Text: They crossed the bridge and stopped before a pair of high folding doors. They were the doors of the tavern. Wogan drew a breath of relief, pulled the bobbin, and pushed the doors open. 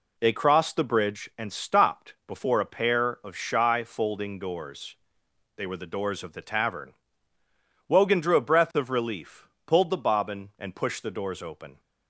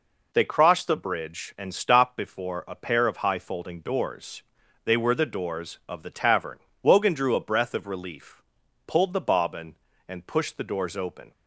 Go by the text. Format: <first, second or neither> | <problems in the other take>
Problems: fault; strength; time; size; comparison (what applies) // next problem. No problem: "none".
second | says "shy" for "high"; at 3.3 s